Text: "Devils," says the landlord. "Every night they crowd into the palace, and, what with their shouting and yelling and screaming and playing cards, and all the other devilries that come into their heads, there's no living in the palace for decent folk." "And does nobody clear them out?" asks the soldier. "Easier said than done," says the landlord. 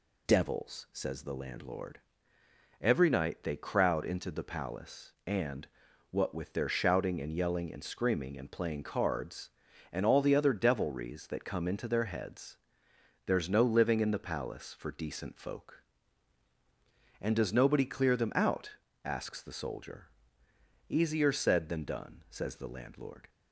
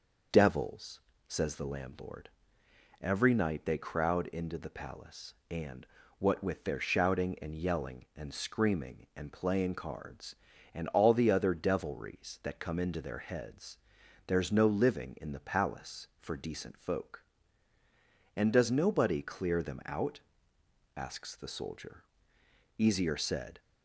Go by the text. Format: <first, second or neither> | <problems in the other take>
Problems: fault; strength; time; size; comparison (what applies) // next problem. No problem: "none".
first | stops before "than done says the landlord"; at 23.5 s